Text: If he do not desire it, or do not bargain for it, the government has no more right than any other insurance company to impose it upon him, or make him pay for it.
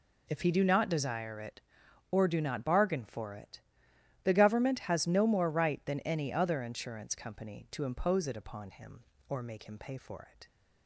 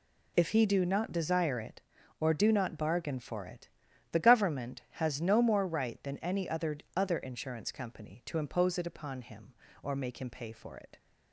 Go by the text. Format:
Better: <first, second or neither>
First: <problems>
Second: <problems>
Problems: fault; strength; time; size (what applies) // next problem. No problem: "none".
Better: first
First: none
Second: says "other" twice; at 6.9 s